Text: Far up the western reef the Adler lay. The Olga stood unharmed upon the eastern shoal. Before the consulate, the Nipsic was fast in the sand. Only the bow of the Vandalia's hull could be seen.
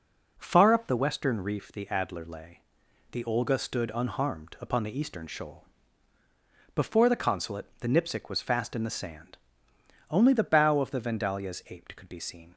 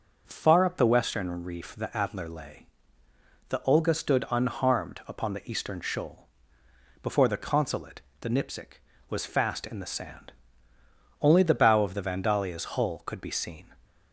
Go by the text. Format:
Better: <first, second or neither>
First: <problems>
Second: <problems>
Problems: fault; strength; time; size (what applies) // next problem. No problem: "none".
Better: second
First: says "aped" for "hull"; at 11.6 s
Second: none